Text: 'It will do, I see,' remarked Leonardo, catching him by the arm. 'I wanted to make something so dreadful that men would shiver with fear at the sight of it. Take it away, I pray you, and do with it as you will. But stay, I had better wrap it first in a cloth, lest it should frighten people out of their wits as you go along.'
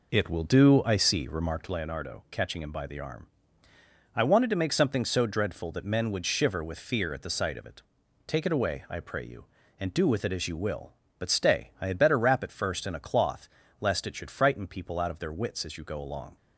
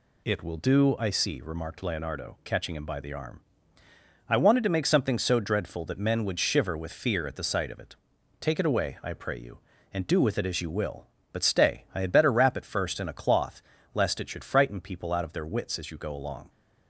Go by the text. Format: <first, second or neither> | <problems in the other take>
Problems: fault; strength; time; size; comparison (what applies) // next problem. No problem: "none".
second | starts louder than the rest; noticeable; until 1.7 s; 4.5 dB